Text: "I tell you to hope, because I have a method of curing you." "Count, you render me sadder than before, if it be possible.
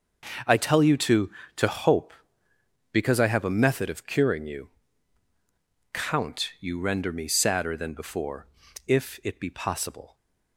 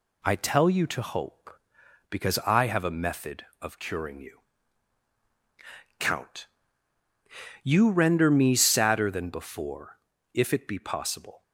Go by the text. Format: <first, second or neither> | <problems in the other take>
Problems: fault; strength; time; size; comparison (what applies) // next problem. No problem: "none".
second | starts louder than the rest; until 1.7 s; 6 dB // says "to" twice; at 1.5 s